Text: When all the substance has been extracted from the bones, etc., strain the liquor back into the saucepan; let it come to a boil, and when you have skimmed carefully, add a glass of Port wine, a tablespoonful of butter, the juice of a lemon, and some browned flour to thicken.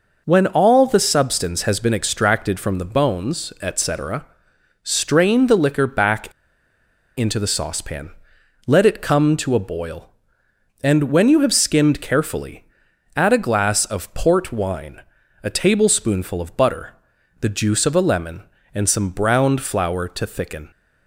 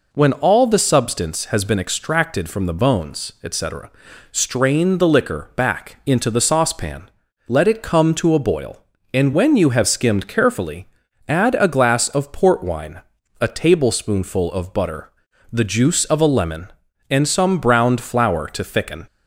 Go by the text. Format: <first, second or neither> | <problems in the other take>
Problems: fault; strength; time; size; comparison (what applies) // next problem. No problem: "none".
second | pauses between "back" and "into"; noticeable; at 6.3 s; 0.85 s long